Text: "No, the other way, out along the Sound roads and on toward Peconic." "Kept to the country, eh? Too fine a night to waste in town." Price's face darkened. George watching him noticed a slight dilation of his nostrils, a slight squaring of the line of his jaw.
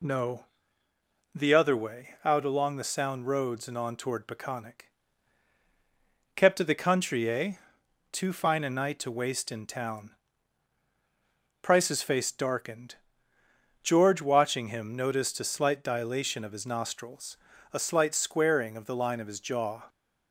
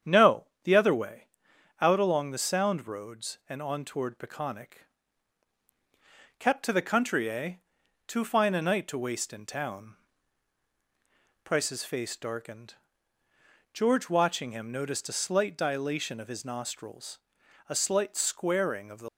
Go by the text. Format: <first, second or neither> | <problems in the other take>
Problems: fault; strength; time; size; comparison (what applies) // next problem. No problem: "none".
first | starts louder than the rest; strong; until 1.2 s; 8.5 dB // stops before "line of his jaw"; at 19.0 s